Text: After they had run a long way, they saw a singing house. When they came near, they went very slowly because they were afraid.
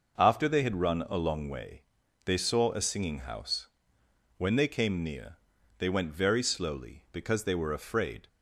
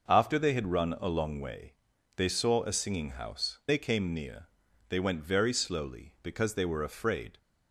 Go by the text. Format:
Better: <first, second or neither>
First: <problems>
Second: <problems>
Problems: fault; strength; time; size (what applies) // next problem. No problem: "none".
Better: first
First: none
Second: skips "When"; at 3.6 s